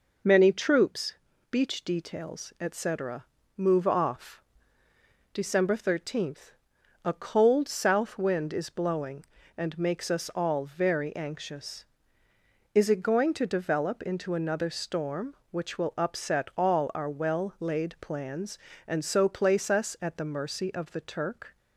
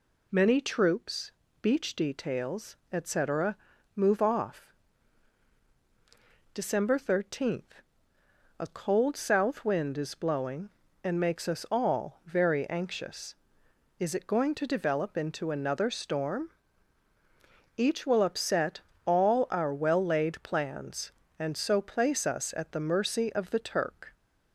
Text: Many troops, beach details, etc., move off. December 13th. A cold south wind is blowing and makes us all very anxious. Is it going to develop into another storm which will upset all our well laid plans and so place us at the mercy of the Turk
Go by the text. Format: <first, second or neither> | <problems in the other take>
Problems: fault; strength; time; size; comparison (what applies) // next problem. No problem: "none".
first | says "each" for "which"; at 17.7 s // pauses between "upset" and "all"; slight; at 18.7 s; 0.26 s long